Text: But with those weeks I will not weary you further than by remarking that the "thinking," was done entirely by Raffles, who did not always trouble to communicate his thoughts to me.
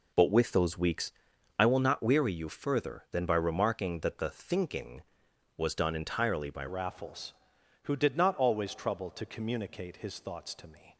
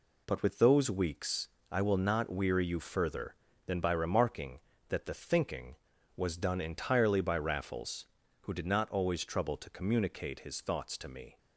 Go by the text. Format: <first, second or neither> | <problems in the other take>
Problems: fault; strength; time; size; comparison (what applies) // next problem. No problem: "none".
second | pauses between "weeks" and "I"; noticeable; at 1.1 s; 0.48 s long; slight in the second // changes voice at "Raffles"; from 6.6 s on; 4.3 s long